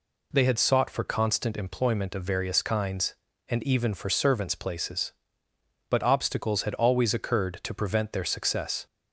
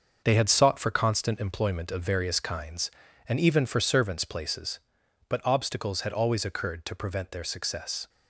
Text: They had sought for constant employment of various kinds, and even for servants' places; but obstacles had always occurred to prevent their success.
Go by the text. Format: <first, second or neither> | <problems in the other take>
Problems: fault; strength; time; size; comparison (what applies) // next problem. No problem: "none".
first | gets quieter; strong; throughout; 7.5 dB